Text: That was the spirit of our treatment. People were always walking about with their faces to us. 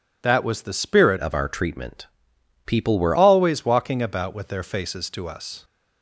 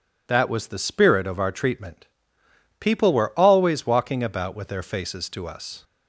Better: second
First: changes voice from "of" to "were"; from 1.1 to 3.1 s; 2.0 s long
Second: none

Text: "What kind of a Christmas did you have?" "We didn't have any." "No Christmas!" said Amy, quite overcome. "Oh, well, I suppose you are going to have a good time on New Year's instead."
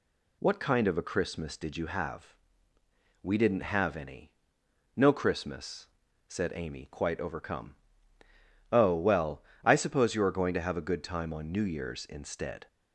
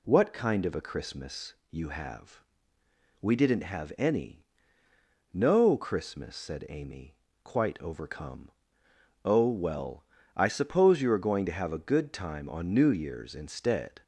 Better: first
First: none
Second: skips "did"; at 1.6 s

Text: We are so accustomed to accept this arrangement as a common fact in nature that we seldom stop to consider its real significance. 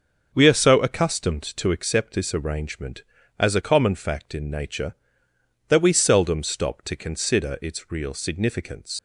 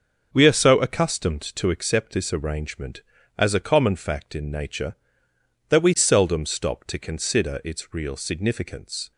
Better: second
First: starts louder than the rest; until 1.3 s; 6.5 dB // leaves "significance" unfinished; at 8.9 s; 95 ms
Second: starts louder than the rest; until 1.3 s; 7 dB

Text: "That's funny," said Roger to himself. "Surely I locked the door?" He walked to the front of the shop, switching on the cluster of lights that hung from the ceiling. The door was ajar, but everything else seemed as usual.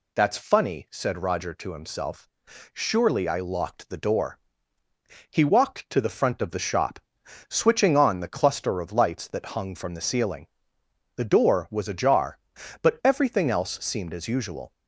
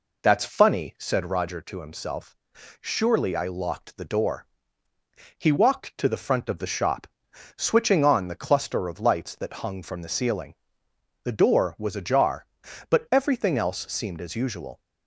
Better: first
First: none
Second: starts louder than the rest; until 1.4 s; 4 dB

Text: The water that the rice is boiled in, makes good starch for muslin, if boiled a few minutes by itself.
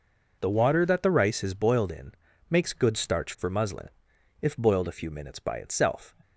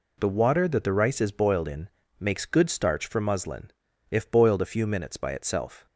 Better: neither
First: none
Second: none

